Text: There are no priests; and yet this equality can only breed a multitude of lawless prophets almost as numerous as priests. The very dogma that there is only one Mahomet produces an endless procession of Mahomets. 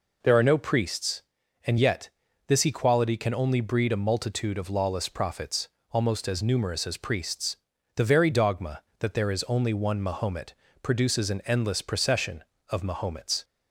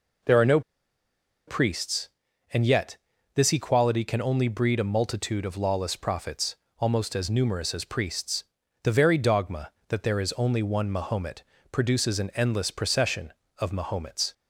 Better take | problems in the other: first | pauses between "no" and "priests"; noticeable; at 0.6 s; 0.86 s long // pauses between "yet" and "this"; at 2.9 s; 0.38 s long; also in the first // pauses between "prophets" and "almost"; slight; at 6.5 s; 0.22 s long; slight in the first // pauses between "Mahomet" and "produces"; slight; at 11.4 s; 0.28 s long; slight in the first

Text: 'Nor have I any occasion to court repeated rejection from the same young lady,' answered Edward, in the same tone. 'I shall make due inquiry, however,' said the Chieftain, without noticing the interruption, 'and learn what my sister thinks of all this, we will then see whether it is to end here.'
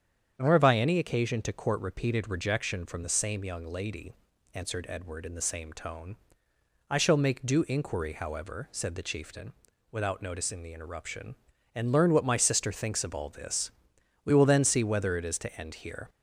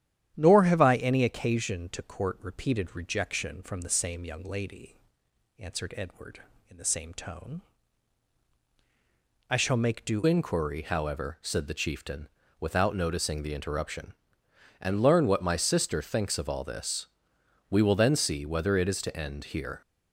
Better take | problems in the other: first | starts louder than the rest; strong; until 1.3 s; 10.5 dB; strong in the first // changes voice at "inquiry"; from 10.2 s on; 9.6 s long

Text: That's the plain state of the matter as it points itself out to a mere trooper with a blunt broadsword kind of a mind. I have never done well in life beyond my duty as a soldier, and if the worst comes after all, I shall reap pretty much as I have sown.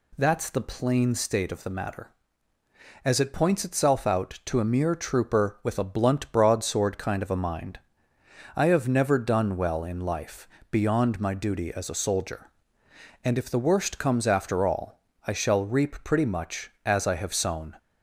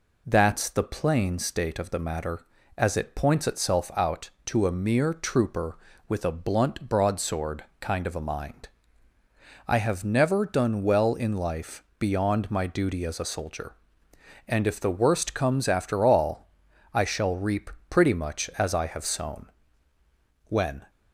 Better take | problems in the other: first | pauses between "broadsword" and "kind"; slight; at 7.6 s; 0.16 s long // pauses between "life" and "beyond"; slight; at 11.8 s; 0.16 s long; slight in the first // pauses between "reap" and "pretty"; slight; at 17.6 s; 0.20 s long // goes on to say "When"; slight; from 20.4 s on; 0.44 s long

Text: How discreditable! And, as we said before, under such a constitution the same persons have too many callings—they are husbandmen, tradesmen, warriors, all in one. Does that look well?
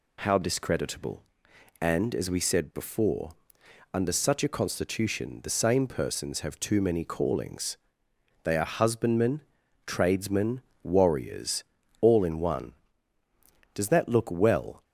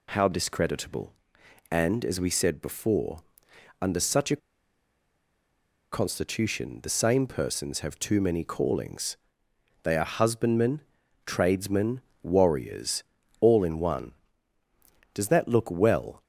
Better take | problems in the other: first | pauses between "a" and "constitution"; strong; at 4.3 s; 1.5 s long

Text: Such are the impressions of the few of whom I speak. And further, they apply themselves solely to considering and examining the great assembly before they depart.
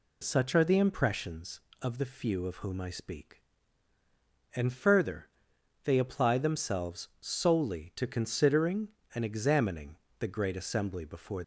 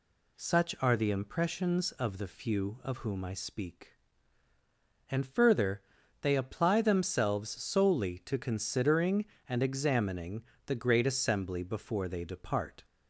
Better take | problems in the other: second | pauses between "examining" and "the"; slight; at 9.9 s; 0.22 s long; slight in the second // stops before "they depart"; at 11.4 s

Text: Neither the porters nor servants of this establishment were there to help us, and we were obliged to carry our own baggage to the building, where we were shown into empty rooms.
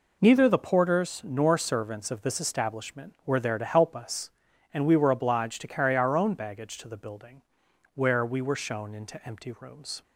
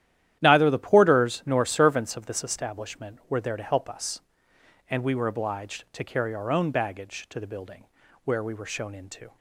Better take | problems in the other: first | starts louder than the rest; strong; until 1.4 s; 11.5 dB // stops before "empty rooms"; at 9.3 s

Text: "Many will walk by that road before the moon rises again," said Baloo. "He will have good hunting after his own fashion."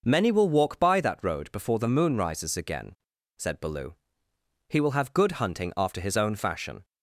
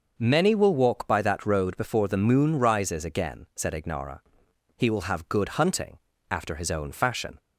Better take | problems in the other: first | starts louder than the rest; noticeable; until 1.1 s; 6 dB // says "Ignara" for "Baloo"; at 3.7 s // pauses between "hunting" and "after"; slight; at 5.9 s; 0.34 s long

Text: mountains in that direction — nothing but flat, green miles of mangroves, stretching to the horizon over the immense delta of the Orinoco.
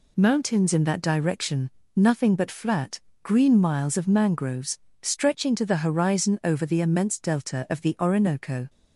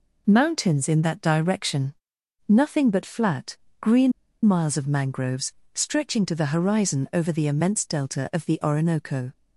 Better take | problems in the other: first | pauses between "green" and "miles"; slight; at 4.1 s; 0.33 s long

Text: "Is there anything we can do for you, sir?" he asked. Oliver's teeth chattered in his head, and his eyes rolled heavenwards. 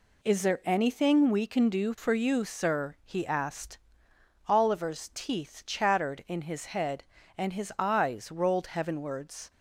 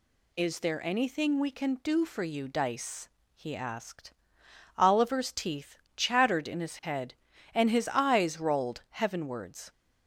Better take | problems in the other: first | says "dice" for "sir"; at 2.4 s // pauses between "teeth" and "chattered"; slight; at 5.7 s; 0.18 s long

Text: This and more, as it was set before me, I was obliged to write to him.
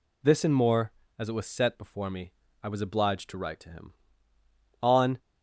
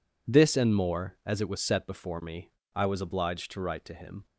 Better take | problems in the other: second | goes on to say "On"; slight; from 4.8 s on; 0.36 s long

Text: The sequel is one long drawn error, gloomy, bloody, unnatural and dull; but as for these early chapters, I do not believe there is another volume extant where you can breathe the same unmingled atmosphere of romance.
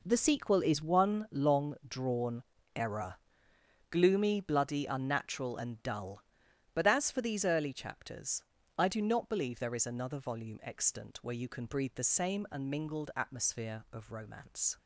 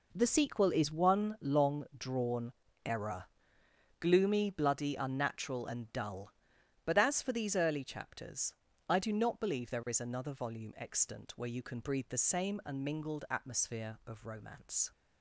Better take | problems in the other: neither | pauses between "drawn" and "error"; slight; the same in both

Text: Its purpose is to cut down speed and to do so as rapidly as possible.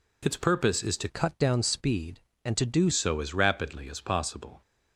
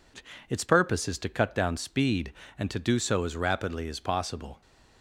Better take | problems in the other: second | changes voice from "cut" to "do"; from 1.0 to 2.8 s; 1.8 s long

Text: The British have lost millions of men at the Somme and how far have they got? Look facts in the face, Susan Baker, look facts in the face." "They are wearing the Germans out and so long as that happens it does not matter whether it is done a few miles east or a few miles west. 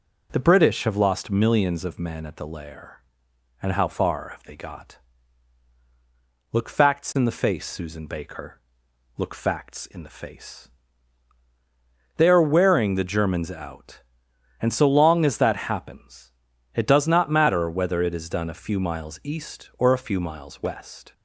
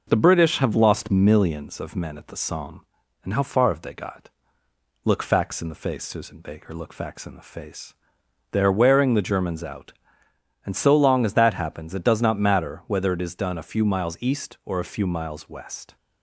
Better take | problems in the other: second | says "Lair" for "Somme"; at 2.4 s // pauses between "happens" and "it"; at 16.3 s; 0.42 s long

